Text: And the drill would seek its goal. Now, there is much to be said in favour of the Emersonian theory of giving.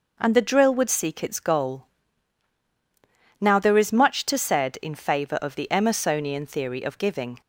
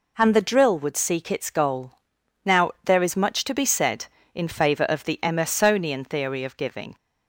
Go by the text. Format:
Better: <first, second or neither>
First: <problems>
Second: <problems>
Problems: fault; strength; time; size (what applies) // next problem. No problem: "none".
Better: second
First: skips "be"; at 4.3 s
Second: none